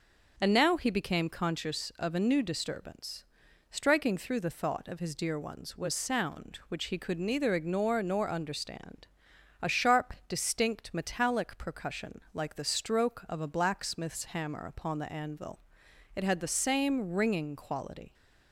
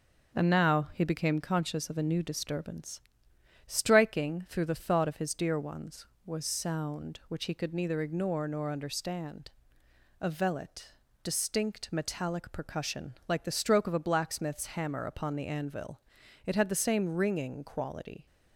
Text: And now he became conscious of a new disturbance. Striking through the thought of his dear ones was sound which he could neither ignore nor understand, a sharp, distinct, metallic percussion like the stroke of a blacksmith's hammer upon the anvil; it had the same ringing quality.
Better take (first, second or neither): first